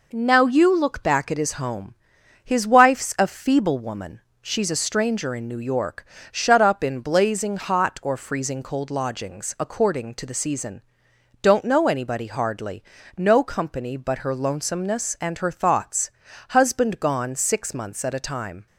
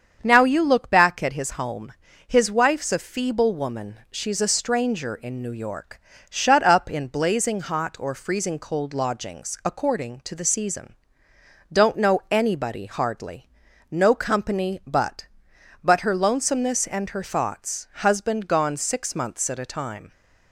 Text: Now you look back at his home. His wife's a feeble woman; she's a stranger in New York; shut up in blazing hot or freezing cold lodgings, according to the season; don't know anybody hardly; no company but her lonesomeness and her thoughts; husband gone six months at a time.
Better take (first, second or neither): first